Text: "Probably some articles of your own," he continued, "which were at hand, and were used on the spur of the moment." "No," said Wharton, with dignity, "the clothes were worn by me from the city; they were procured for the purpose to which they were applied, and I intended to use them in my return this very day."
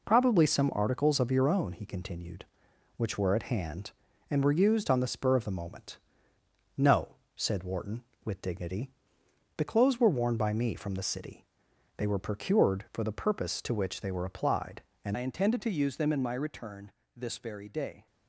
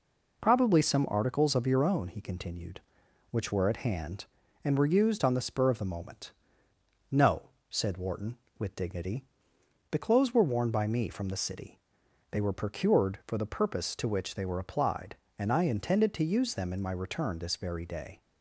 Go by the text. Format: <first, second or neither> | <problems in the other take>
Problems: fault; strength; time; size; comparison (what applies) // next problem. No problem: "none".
second | changes voice at "I"; from 15.1 s on; 2.9 s long // pauses between "return" and "this"; slight; at 16.8 s; 0.26 s long